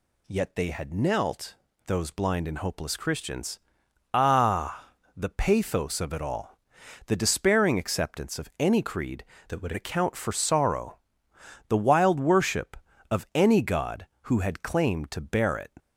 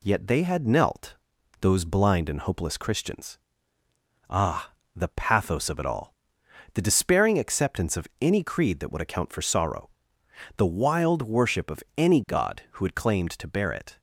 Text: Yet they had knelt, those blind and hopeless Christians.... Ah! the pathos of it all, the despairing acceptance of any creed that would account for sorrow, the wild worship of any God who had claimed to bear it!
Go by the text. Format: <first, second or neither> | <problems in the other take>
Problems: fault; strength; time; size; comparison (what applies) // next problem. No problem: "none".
second | changes voice from "that" to "would"; from 9.4 to 9.7 s; 0.3 s long